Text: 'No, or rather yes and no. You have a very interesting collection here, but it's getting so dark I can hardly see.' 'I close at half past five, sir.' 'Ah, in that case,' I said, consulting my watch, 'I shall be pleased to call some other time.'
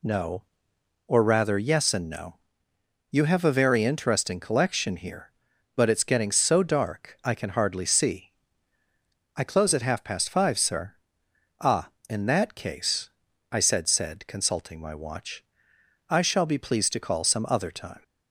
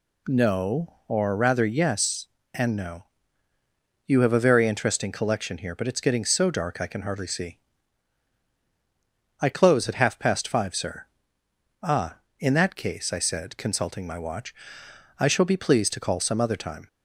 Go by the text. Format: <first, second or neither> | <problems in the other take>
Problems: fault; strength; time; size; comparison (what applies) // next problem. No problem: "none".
second | says "said" twice; at 13.8 s